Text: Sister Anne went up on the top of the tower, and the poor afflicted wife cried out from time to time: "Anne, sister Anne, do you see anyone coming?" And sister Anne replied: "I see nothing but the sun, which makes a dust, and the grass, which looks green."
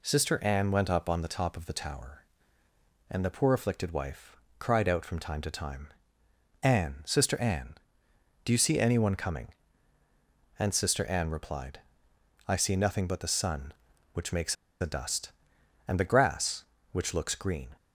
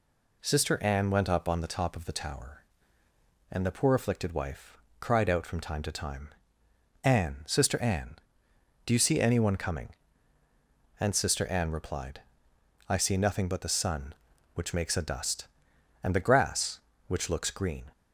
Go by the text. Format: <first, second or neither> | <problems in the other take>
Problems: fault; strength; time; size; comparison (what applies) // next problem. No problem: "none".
second | pauses between "wife" and "cried"; slight; at 4.3 s; 0.22 s long; slight in the second // pauses between "makes" and "a"; slight; at 14.5 s; 0.26 s long